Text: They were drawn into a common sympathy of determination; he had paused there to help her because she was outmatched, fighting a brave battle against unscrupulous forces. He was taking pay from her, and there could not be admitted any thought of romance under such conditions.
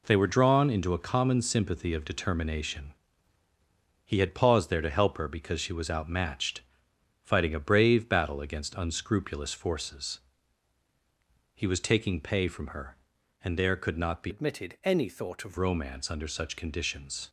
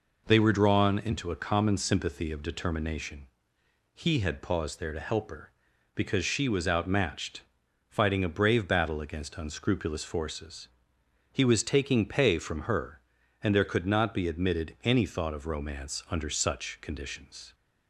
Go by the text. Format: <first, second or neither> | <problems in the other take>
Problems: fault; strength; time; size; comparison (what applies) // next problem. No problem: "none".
second | changes voice from "admitted" to "of"; from 14.2 to 15.5 s; 1.3 s long